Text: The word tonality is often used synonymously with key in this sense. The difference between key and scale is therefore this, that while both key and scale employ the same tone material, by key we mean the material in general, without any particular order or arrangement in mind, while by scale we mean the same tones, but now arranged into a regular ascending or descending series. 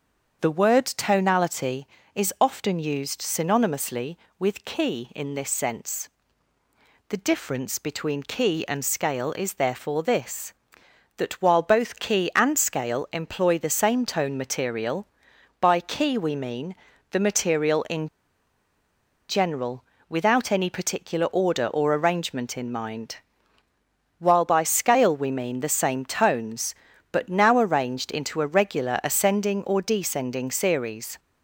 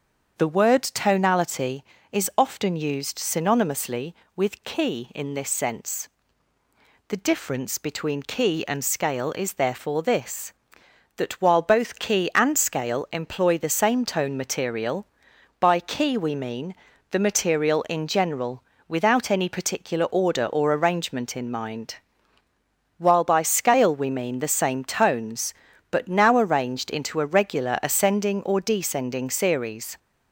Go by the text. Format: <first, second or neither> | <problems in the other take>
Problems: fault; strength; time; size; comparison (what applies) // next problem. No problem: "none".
second | starts louder than the rest; until 1.4 s; 7 dB; also in the second // pauses between "mean" and "the"; slight; at 16.7 s; 0.36 s long; slight in the second // pauses between "in" and "general"; at 18.0 s; 1.2 s long